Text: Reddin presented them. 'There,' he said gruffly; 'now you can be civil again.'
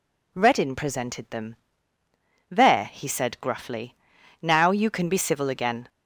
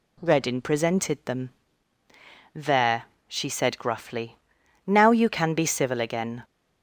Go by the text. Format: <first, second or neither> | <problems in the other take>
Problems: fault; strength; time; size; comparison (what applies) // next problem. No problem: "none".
first | says "she" for "he"; at 3.2 s